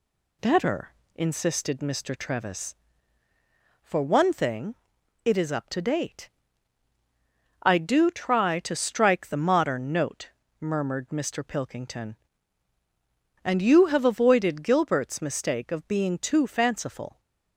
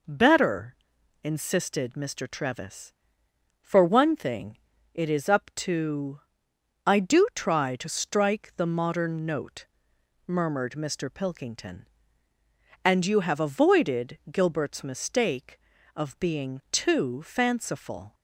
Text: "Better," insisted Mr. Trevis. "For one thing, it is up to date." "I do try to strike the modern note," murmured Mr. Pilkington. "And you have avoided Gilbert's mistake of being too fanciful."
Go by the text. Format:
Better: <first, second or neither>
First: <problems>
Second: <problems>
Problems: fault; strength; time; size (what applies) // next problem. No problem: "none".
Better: first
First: none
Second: skips "date"; at 6.5 s